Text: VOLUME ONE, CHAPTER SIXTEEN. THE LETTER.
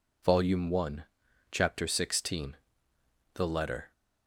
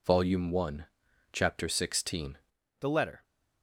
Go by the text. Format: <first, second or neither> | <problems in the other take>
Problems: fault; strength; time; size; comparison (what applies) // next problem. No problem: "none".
first | changes voice at "THE"; from 2.8 s on; 0.4 s long